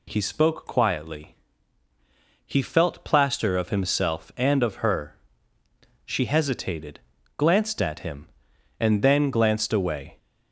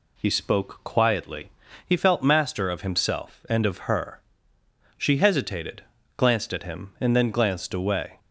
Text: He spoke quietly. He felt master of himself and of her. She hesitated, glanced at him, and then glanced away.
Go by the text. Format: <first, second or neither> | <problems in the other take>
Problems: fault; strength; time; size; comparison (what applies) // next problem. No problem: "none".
second | says "plaster" for "master"; at 3.0 s